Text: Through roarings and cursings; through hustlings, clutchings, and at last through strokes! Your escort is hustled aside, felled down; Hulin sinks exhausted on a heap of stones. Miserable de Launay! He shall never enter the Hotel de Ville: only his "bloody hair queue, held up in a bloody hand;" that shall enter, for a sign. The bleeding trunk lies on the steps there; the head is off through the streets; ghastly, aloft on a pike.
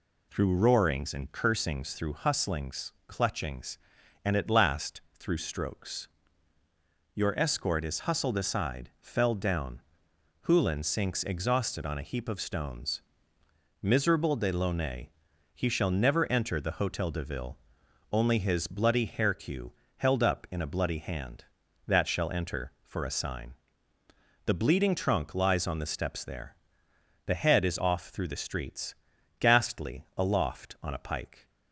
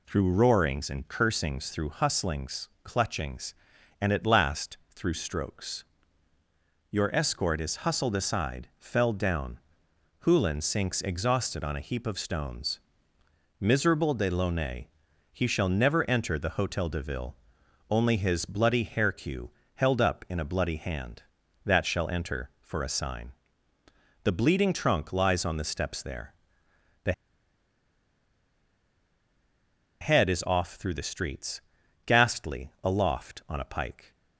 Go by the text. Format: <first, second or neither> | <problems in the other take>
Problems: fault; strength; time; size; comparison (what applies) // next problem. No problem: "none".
first | pauses between "the" and "head"; strong; at 27.1 s; 2.8 s long